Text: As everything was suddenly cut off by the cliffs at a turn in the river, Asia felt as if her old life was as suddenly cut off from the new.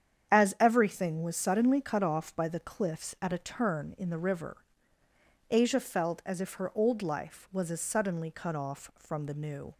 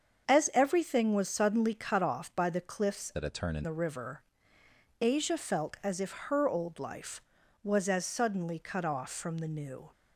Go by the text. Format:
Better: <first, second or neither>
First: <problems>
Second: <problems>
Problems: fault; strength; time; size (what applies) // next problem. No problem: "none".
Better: first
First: starts louder than the rest; strong; until 1.3 s; 8.5 dB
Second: starts louder than the rest; until 1.3 s; 7 dB // changes voice from "at" to "in"; from 3.1 to 3.6 s; 0.5 s long